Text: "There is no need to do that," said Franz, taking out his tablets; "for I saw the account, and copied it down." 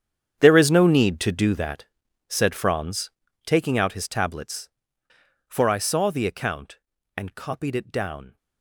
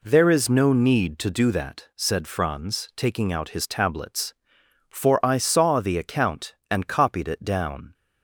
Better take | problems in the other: second | gets quieter; strong; throughout; 17 dB

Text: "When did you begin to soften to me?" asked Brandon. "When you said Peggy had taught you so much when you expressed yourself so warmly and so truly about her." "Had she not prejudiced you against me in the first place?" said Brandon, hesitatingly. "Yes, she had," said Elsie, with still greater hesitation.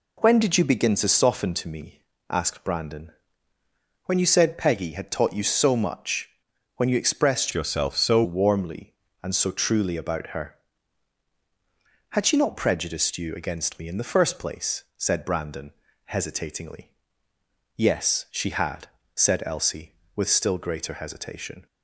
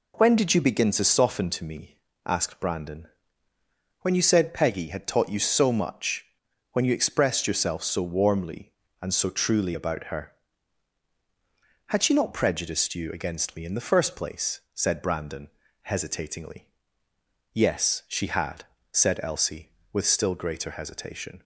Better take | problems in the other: second | pauses between "much" and "when"; noticeable; at 6.2 s; 0.46 s long; noticeable in the second // changes voice from "yourself" to "so"; from 7.5 to 8.2 s; 0.7 s long

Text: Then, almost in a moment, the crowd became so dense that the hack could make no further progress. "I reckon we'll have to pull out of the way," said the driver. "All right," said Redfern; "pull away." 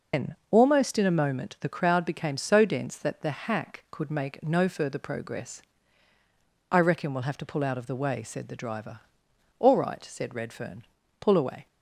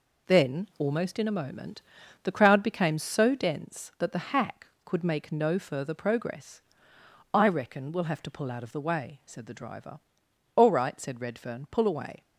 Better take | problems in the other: second | loses the start of "Then"; at 0.1 s; 170 ms

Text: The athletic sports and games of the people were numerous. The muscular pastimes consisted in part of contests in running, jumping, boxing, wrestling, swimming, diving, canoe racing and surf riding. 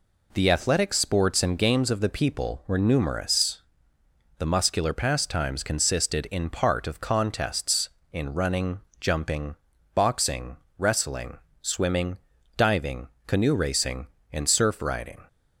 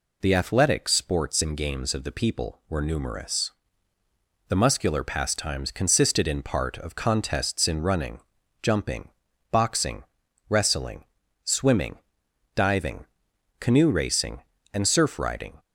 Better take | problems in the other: neither | none

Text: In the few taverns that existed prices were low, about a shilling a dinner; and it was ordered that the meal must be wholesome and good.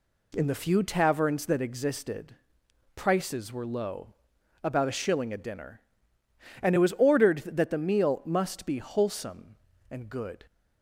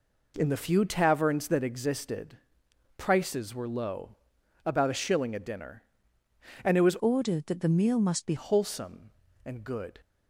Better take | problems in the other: first | pauses between "existed" and "prices"; noticeable; at 2.3 s; 0.60 s long; noticeable in the first // changes voice from "ordered" to "be"; from 7.0 to 8.3 s; 1.3 s long

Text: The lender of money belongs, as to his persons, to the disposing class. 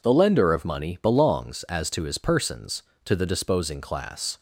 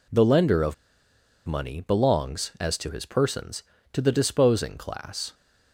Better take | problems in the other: first | pauses between "of" and "money"; noticeable; at 0.7 s; 0.71 s long

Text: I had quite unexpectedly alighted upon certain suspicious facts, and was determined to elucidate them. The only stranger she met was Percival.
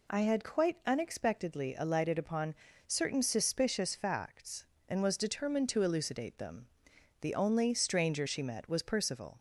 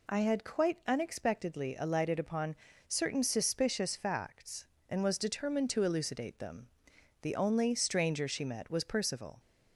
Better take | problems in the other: neither | pauses between "upon" and "certain"; slight; the same in both

